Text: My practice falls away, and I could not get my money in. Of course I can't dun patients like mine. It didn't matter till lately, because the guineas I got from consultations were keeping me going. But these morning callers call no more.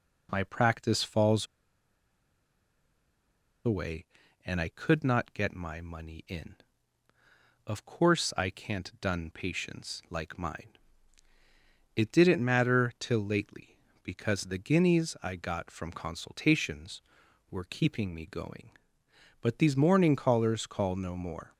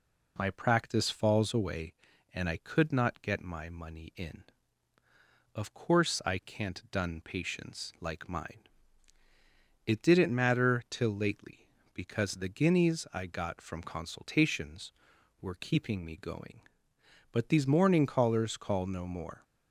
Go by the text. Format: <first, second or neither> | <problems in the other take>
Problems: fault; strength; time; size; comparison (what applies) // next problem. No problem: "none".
second | pauses between "falls" and "away"; strong; at 1.4 s; 2.1 s long